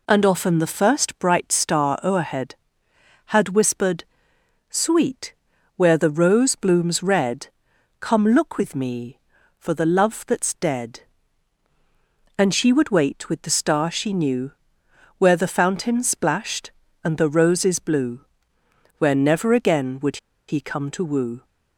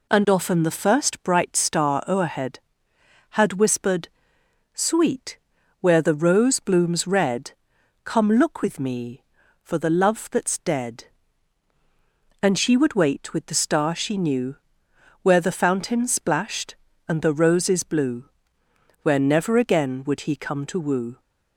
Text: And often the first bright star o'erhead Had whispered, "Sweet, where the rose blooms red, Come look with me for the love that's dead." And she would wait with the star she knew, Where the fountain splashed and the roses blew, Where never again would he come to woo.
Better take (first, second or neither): second